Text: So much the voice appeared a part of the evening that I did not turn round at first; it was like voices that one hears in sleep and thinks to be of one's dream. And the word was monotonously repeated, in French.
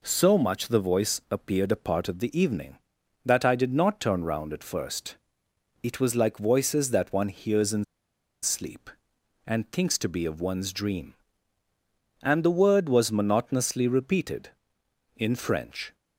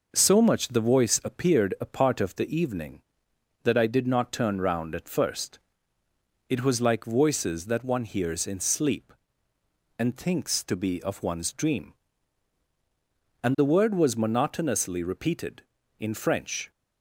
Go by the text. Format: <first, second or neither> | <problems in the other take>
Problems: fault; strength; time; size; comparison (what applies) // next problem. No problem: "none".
second | pauses between "in" and "sleep"; noticeable; at 7.8 s; 0.58 s long